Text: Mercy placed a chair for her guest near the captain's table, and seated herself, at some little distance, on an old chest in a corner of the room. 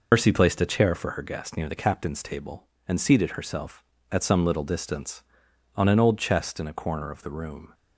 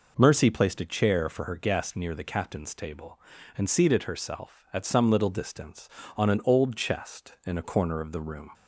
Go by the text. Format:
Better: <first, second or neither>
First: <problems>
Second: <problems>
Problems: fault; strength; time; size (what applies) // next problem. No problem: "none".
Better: second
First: loses the start of "Mercy"; at 0.1 s; 105 ms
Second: none